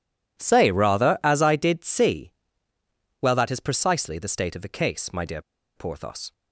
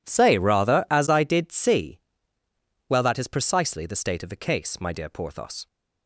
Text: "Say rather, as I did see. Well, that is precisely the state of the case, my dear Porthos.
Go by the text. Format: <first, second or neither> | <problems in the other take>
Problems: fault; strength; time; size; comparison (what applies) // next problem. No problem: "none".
second | pauses between "dear" and "Porthos"; slight; at 5.4 s; 0.35 s long